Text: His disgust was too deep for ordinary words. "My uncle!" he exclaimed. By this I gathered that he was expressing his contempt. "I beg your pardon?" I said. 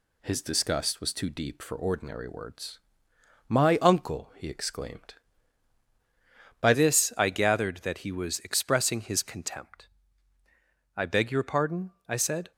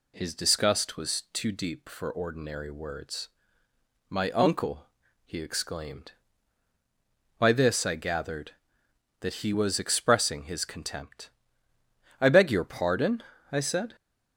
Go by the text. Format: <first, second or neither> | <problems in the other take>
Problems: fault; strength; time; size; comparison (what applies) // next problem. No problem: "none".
second | changes voice at "this"; from 6.7 s on; 5.8 s long